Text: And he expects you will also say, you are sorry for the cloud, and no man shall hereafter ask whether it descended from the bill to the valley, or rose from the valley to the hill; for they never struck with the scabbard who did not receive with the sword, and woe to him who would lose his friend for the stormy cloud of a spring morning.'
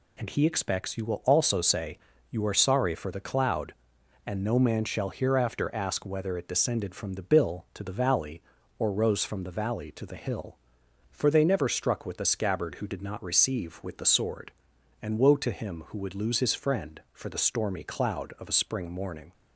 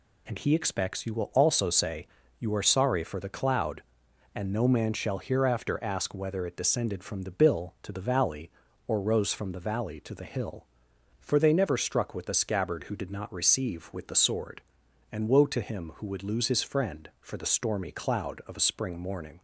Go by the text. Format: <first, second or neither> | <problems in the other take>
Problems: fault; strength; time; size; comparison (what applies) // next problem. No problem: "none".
neither | none